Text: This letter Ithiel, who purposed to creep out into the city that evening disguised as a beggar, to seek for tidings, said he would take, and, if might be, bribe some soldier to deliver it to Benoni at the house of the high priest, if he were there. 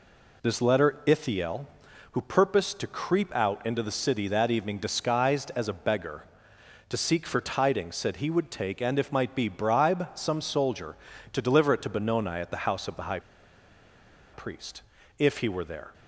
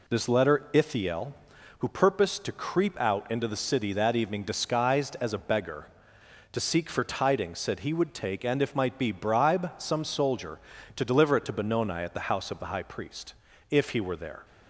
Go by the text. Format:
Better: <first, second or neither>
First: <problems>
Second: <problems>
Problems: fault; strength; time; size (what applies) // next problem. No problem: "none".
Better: second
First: pauses between "high" and "priest"; at 13.1 s; 1.1 s long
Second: none